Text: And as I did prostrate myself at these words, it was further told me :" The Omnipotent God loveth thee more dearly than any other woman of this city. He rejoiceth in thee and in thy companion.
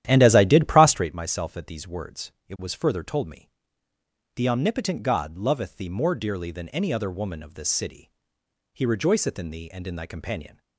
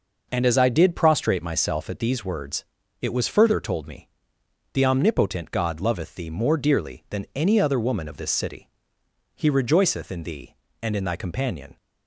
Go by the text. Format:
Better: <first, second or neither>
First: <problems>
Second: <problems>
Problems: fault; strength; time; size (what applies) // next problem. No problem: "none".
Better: second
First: starts louder than the rest; strong; until 1.1 s; 12 dB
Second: none